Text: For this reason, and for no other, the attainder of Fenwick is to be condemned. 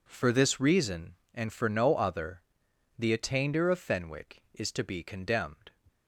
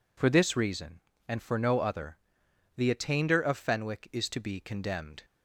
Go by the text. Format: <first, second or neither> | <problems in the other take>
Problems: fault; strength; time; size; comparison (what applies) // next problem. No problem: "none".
neither | none